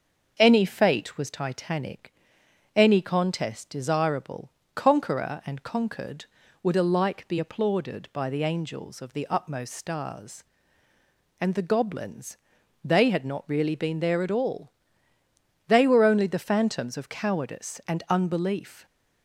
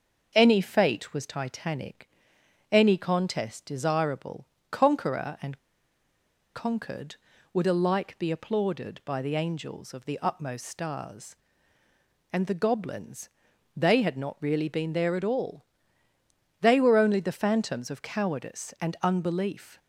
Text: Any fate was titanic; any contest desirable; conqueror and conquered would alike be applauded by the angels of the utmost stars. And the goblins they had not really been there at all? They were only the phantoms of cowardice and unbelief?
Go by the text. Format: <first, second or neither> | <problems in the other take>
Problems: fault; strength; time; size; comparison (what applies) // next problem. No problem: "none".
first | starts louder than the rest; until 1.3 s; 6 dB; also in the first // pauses between "and" and "conquered"; noticeable; at 5.5 s; 0.95 s long // pauses between "goblins" and "they"; noticeable; at 13.2 s; 0.48 s long; noticeable in the first